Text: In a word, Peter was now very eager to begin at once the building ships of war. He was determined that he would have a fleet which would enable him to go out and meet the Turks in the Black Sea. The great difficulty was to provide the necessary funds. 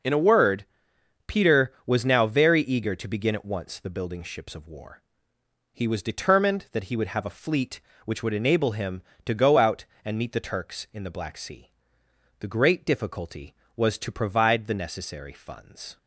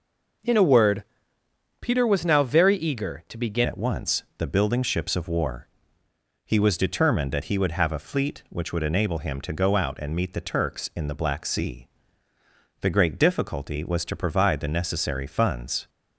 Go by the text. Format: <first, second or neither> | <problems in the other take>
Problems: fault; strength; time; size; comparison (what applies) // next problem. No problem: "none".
first | changes voice at "at"; from 3.6 s on; 12.2 s long // pauses between "once" and "the"; slight; at 4.2 s; 0.16 s long